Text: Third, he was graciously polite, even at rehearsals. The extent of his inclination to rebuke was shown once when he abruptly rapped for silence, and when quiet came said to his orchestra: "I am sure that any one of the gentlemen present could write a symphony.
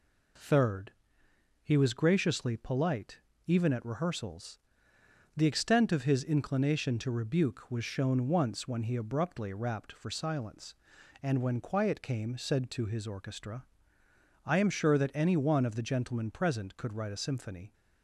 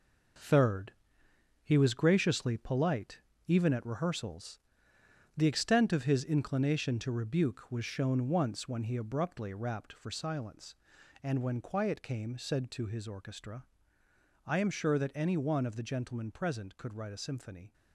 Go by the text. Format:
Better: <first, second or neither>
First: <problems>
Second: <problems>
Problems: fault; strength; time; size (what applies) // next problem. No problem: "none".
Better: first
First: none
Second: gets quieter; strong; throughout; 8 dB